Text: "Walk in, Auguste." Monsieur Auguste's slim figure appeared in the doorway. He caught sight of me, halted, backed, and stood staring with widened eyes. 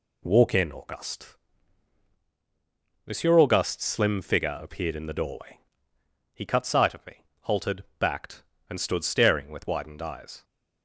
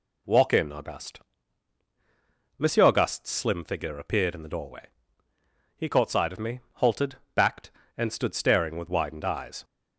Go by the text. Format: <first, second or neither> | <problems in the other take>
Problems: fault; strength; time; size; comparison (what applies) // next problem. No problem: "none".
second | says "cut" for "caught"; at 6.4 s